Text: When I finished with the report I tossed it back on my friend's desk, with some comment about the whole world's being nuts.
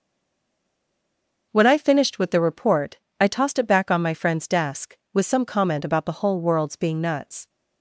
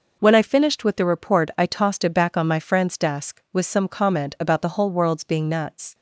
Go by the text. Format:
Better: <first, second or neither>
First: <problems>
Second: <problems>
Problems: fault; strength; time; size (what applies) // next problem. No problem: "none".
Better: second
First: stays silent before the first word; noticeable; until 1.5 s; 1.5 s long // starts louder than the rest; noticeable; until 2.5 s; 6 dB // pauses between "report" and "I"; slight; at 2.9 s; 0.20 s long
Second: none